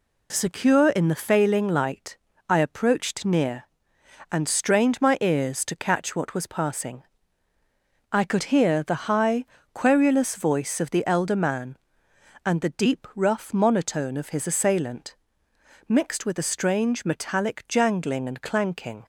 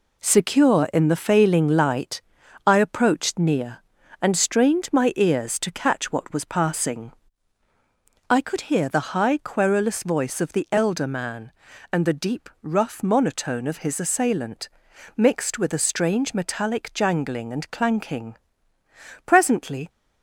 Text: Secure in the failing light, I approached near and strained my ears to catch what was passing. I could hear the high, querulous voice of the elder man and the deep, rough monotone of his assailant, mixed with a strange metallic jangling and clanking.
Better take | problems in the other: first | goes on to say "Presently"; noticeable; from 19.2 s on; 0.64 s long

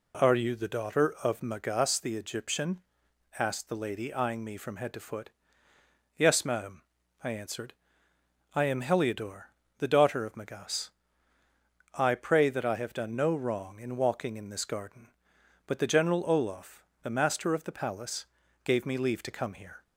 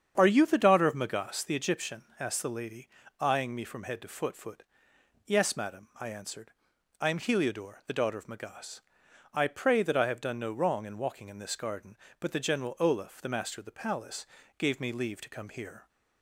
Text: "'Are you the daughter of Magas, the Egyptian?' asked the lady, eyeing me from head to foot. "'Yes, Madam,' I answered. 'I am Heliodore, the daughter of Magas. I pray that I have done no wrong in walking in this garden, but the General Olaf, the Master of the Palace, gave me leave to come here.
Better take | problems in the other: first | starts louder than the rest; strong; until 1.1 s; 8 dB // says "foot" twice; at 4.3 s

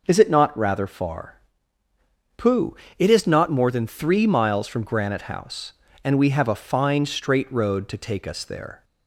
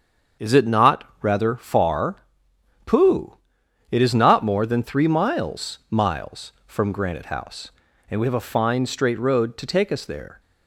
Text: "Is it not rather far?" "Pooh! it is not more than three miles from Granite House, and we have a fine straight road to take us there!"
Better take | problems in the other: first | starts louder than the rest; until 1.5 s; 7 dB // pauses between "not" and "rather"; slight; at 1.0 s; 0.18 s long // says "miles" twice; at 5.9 s

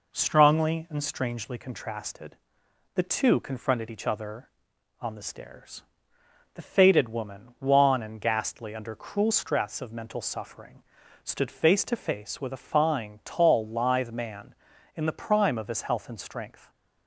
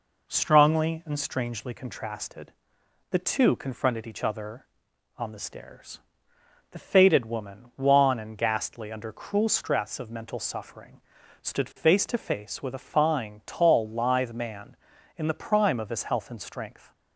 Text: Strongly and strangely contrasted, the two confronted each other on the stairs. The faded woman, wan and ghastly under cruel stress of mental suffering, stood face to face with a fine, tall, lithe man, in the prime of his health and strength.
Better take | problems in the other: neither | none

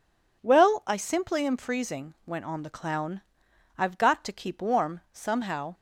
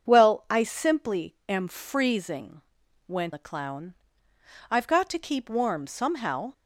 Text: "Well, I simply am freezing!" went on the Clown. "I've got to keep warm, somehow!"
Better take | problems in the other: first | starts louder than the rest; until 1.1 s; 7 dB // skips "on"; at 3.3 s

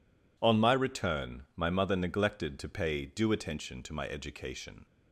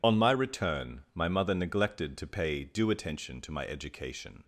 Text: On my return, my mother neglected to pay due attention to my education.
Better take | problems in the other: first | loses the start of "On"; at 0.0 s; 65 ms

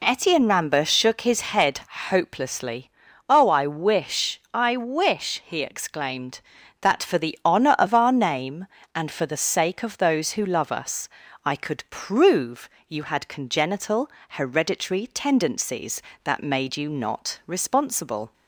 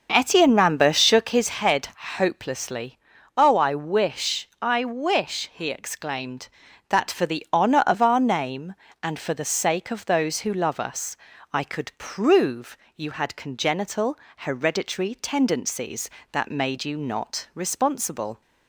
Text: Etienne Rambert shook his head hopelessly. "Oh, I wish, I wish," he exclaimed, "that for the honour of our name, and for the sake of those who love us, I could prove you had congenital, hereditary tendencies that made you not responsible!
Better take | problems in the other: first | starts louder than the rest; noticeable; until 1.5 s; 6 dB // pauses between "head" and "hopelessly"; slight; at 1.8 s; 0.28 s long; slight in the first // pauses between "prove" and "you"; slight; at 12.7 s; 0.20 s long; slight in the first

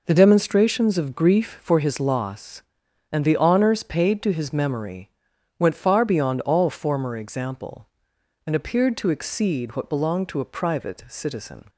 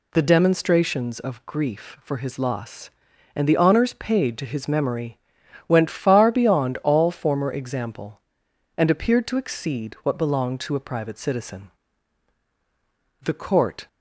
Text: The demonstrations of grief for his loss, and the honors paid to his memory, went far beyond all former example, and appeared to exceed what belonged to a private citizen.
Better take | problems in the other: first | goes on to say "The court"; noticeable; from 13.2 s on; 0.64 s long

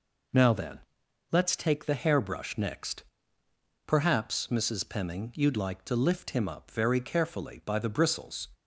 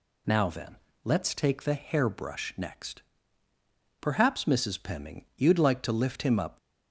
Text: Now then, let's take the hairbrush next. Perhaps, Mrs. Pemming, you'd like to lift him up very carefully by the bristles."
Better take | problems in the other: first | stops before "very carefully by the bristles"; at 6.5 s

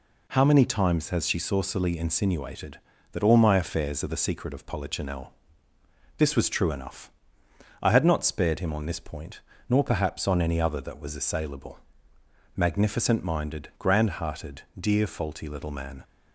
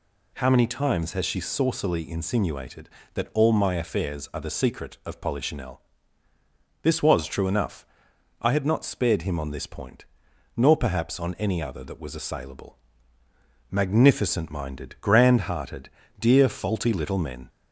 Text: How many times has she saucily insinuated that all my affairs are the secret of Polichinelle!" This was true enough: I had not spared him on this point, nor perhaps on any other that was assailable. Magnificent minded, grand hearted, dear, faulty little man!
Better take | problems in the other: first | says "men" for "man"; at 17.1 s

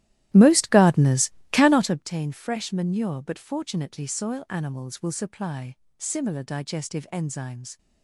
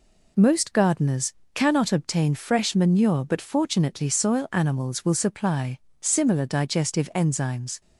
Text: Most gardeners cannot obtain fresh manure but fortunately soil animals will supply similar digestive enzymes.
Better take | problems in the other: second | starts louder than the rest; strong; until 2.1 s; 14 dB // pauses between "gardeners" and "cannot"; slight; at 1.2 s; 0.22 s long; slight in the second // pauses between "supply" and "similar"; slight; at 5.7 s; 0.22 s long; slight in the second

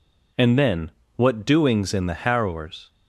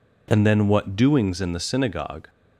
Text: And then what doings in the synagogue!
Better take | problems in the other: second | pauses between "then" and "what"; slight; at 0.8 s; 0.26 s long // says "harrowers" for "synagogue"; at 2.1 s

